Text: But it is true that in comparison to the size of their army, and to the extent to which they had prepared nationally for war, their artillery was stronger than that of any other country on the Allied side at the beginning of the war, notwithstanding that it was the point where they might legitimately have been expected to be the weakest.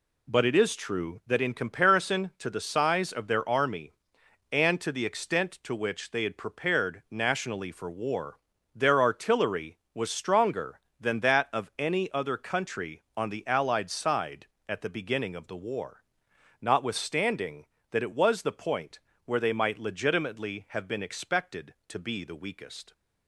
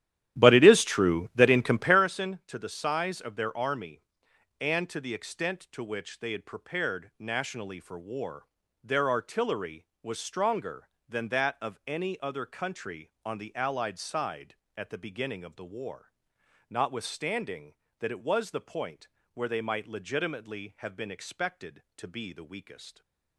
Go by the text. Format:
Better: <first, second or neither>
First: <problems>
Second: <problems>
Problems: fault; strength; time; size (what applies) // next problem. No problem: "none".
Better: first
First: pauses between "point" and "where"; slight; at 18.9 s; 0.26 s long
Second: starts louder than the rest; strong; until 2.0 s; 12.5 dB // pauses between "point" and "where"; slight; at 19.0 s; 0.26 s long